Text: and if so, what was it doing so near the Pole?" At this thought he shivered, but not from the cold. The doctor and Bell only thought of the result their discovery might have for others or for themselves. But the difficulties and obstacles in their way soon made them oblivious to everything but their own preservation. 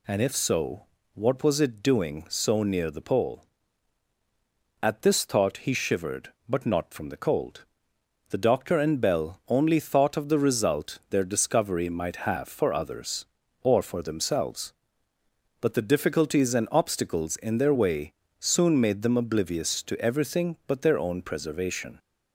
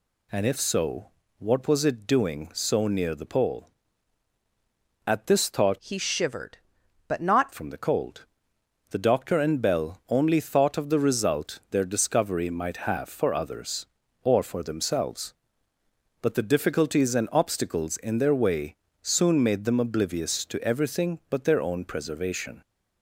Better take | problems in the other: first | changes voice from "he" to "not"; from 5.7 to 7.5 s; 1.8 s long // pauses between "way" and "soon"; slight; at 18.7 s; 0.24 s long; slight in the first

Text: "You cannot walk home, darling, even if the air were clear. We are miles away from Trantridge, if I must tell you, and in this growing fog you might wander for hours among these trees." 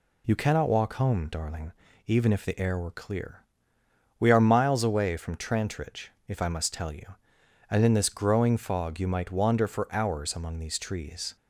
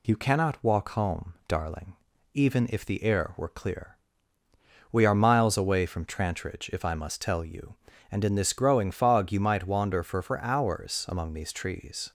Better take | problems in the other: first | says "for" twice; at 10.2 s

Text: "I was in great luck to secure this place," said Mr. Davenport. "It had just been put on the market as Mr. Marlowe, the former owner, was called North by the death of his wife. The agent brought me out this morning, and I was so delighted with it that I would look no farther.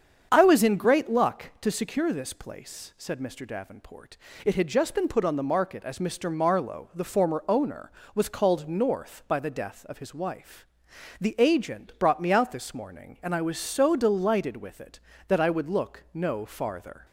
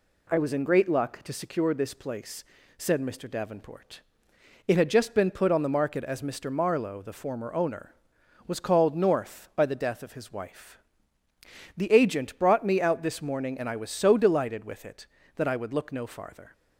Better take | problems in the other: second | starts louder than the rest; strong; until 1.7 s; 7.5 dB

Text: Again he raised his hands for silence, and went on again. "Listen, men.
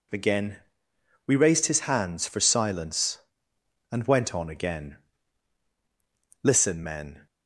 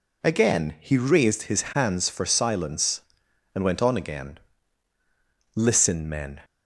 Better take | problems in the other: second | says "we" for "he"; at 1.2 s

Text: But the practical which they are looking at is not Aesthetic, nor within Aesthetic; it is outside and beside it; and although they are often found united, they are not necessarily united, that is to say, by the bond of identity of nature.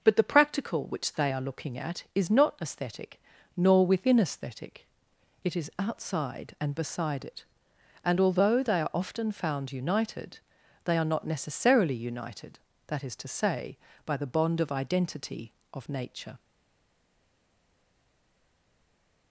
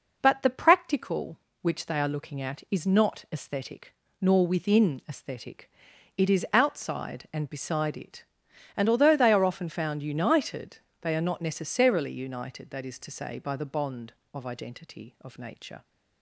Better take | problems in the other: second | stays silent after the last word; strong; from 16.3 s on; 3.0 s long

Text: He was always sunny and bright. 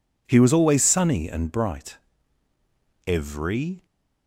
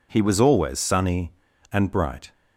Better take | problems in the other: second | goes on to say "Every"; noticeable; from 3.0 s on; 0.80 s long

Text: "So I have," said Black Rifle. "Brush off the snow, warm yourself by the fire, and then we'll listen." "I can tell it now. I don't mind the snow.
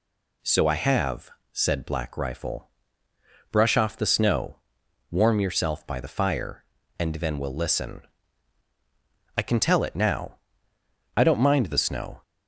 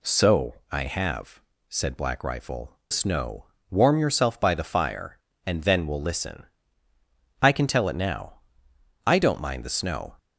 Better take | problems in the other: first | pauses between "So" and "I"; slight; at 0.5 s; 0.16 s long // skips "Brush off the"; at 2.8 s

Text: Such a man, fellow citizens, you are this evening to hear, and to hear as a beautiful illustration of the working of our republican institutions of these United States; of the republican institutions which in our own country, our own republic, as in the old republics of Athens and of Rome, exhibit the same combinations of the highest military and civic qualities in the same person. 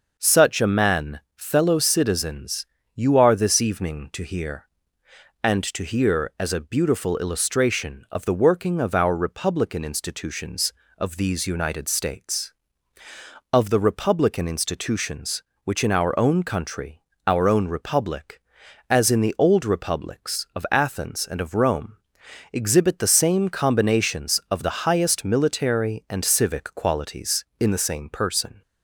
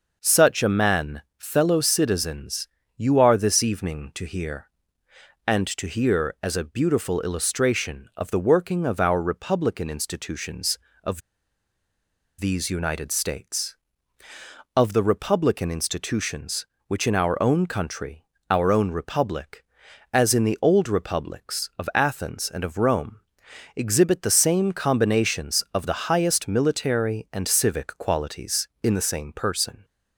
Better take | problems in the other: first | pauses between "of" and "these"; at 11.2 s; 1.1 s long

